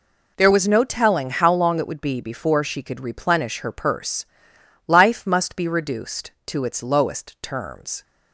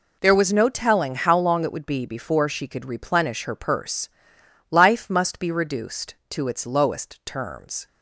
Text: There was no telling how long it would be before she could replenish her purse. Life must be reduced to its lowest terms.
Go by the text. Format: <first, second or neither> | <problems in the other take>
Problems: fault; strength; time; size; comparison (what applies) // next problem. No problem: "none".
neither | none